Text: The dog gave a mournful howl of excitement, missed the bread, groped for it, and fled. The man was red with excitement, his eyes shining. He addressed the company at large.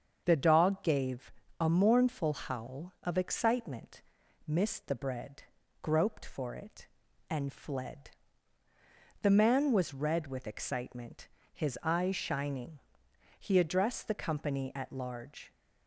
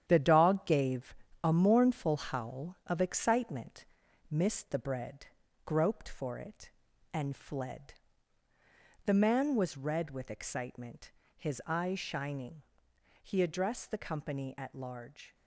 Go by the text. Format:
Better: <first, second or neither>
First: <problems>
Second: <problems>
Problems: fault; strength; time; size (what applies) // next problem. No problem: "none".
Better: first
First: starts louder than the rest; until 1.2 s; 7 dB // pauses between "gave" and "a"; slight; at 1.3 s; 0.27 s long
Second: gets quieter; strong; throughout; 7.5 dB // starts louder than the rest; strong; until 1.0 s; 9.5 dB // pauses between "gave" and "a"; slight; at 1.1 s; 0.28 s long